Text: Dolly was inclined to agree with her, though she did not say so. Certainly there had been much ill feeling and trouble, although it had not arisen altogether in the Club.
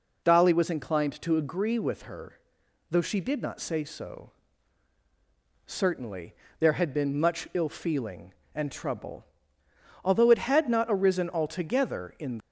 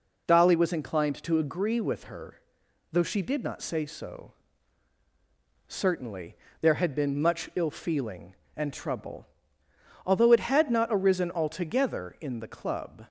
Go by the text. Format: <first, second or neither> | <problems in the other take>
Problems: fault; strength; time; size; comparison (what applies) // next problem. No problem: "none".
second | pauses between "Certainly" and "there"; slight; at 6.3 s; 0.26 s long; slight in the second // stops before "the Club"; at 12.3 s